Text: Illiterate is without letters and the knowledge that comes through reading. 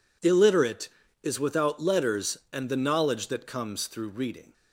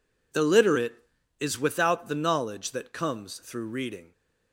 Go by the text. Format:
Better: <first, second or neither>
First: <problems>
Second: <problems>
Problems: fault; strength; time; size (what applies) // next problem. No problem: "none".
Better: first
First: none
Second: skips "letters and"; at 2.0 s